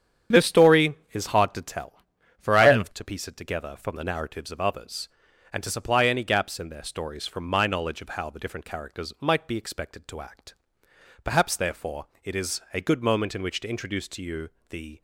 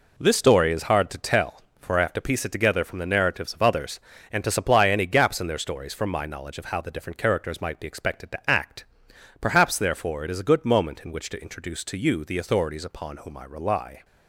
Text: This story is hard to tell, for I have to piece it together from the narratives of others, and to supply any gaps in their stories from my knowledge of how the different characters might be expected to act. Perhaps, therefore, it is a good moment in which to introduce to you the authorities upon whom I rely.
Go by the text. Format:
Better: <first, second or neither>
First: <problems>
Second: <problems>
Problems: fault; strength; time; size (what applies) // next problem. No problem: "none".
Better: second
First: starts louder than the rest; strong; until 1.4 s; 8.5 dB // pauses between "you" and "the"; slight; at 14.4 s; 0.22 s long // stops before "authorities upon whom I rely"; at 14.9 s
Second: none